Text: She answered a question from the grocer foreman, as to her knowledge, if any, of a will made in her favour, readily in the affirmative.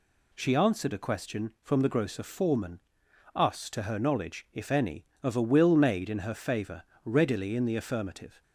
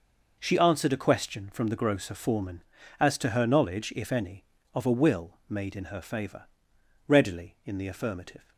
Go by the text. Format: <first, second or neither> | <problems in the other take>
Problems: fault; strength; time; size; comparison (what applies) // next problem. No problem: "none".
second | says "us" for "as"; at 3.3 s